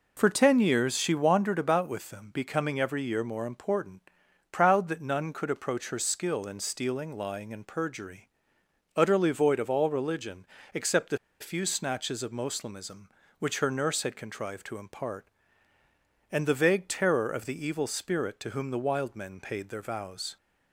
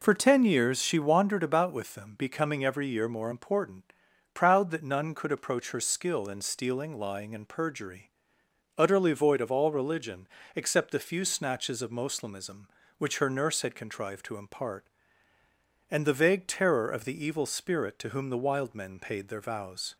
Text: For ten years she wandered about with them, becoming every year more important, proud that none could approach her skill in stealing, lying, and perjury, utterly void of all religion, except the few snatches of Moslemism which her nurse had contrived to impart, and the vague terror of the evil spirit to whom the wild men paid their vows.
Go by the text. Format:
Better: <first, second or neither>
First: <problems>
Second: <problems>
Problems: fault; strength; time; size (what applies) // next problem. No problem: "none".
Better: second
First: pauses between "the" and "few"; slight; at 11.1 s; 0.22 s long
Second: none